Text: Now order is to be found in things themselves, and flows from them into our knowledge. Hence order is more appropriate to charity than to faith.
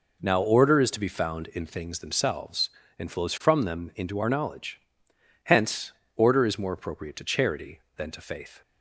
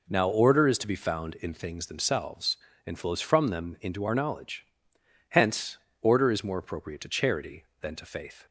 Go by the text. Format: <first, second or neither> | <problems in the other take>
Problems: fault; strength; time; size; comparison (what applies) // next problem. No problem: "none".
neither | pauses between "Hence" and "order"; slight; the same in both